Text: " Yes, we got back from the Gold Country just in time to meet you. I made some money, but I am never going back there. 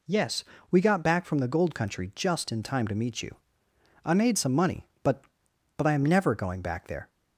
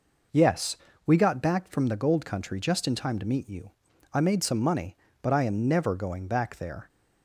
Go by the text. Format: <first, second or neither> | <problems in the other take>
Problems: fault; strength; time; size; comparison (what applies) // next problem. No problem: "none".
second | says "but" twice; at 5.7 s